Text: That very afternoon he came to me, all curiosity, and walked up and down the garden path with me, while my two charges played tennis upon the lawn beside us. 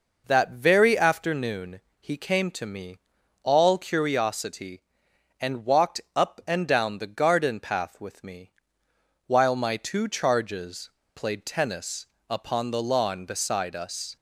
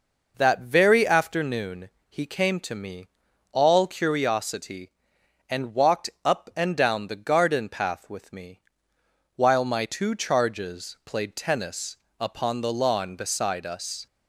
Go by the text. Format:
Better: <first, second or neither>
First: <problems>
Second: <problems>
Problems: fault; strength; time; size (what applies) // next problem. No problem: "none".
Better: second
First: pauses between "afternoon" and "he"; slight; at 1.8 s; 0.18 s long // pauses between "walked" and "up"; slight; at 5.9 s; 0.16 s long // pauses between "charges" and "played"; slight; at 10.8 s; 0.25 s long // pauses between "tennis" and "upon"; slight; at 12.0 s; 0.24 s long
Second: pauses between "afternoon" and "he"; slight; at 1.9 s; 0.18 s long // pauses between "walked" and "up"; slight; at 6.0 s; 0.16 s long // pauses between "tennis" and "upon"; slight; at 11.9 s; 0.24 s long